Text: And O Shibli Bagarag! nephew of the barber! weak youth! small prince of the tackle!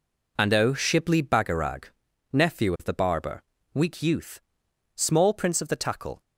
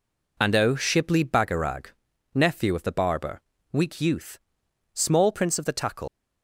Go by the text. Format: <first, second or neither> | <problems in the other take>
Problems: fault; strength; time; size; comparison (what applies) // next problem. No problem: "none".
first | leaves "tackle" unfinished; at 6.0 s; 95 ms